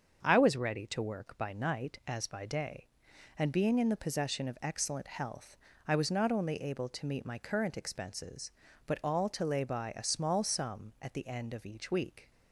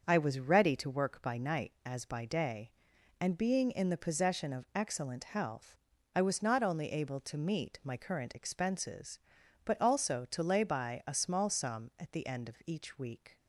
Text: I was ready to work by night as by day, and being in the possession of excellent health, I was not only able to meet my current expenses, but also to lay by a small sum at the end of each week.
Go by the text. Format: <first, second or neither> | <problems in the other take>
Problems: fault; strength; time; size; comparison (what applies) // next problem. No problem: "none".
second | starts louder than the rest; until 1.2 s; 6.5 dB; also in the second // says "all" for "also"; at 9.0 s